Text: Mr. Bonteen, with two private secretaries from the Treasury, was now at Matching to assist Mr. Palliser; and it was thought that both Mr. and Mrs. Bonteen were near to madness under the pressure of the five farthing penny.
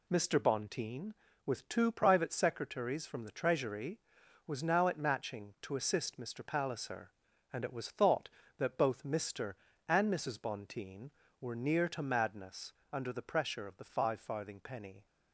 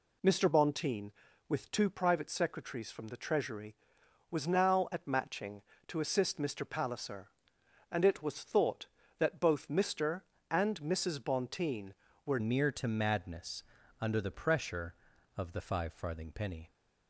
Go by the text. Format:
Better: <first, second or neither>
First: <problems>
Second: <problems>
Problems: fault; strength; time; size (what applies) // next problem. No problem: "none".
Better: first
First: pauses between "madness" and "under"; slight; at 12.7 s; 0.20 s long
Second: changes voice at "near"; from 12.3 s on; 4.3 s long // pauses between "madness" and "under"; slight; at 13.6 s; 0.36 s long